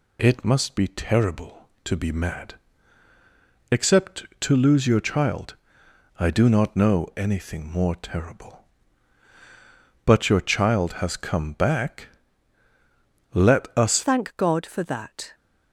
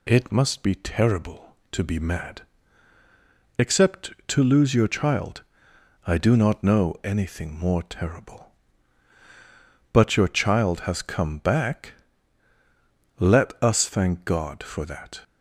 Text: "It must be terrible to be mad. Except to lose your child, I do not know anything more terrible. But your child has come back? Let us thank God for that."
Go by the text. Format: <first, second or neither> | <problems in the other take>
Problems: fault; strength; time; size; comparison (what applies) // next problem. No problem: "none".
second | changes voice at "thank"; from 14.0 s on; 1.3 s long